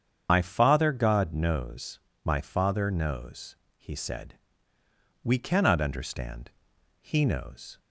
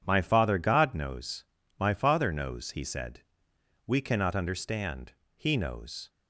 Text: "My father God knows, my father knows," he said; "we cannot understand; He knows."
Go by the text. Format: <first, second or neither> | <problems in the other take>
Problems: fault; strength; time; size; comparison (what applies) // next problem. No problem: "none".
second | loses the start of "My"; at 0.2 s; 90 ms // starts louder than the rest; strong; until 1.3 s; 8 dB